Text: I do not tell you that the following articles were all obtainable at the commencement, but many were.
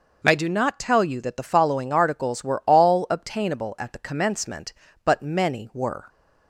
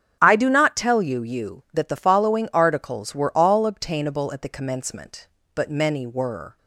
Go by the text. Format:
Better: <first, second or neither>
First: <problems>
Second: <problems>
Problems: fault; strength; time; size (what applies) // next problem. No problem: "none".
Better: first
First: none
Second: starts louder than the rest; strong; until 1.2 s; 8 dB // says "you" twice; at 1.2 s